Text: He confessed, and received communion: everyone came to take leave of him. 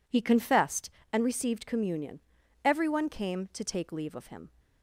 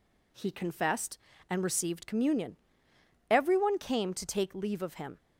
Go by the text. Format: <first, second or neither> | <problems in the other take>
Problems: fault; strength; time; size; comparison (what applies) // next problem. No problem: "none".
neither | none